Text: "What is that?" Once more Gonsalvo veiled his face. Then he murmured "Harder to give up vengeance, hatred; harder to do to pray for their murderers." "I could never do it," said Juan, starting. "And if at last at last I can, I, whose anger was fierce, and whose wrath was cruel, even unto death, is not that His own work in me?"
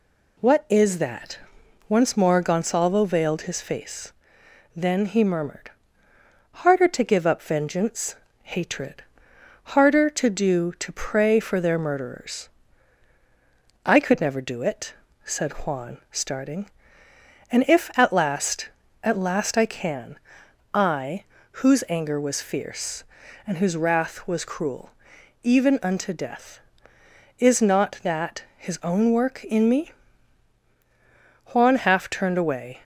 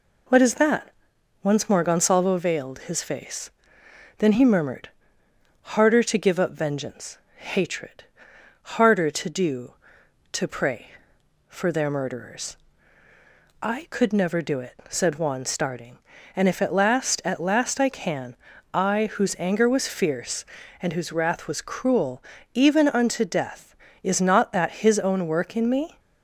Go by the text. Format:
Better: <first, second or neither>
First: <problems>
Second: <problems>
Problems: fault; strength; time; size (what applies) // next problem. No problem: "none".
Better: second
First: pauses between "murmured" and "Harder"; noticeable; at 5.7 s; 0.92 s long // pauses between "that" and "His"; slight; at 28.4 s; 0.16 s long // goes on to say "Juan half turned away"; noticeable; from 31.5 s on; 1.2 s long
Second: pauses between "murmured" and "Harder"; noticeable; at 4.8 s; 0.72 s long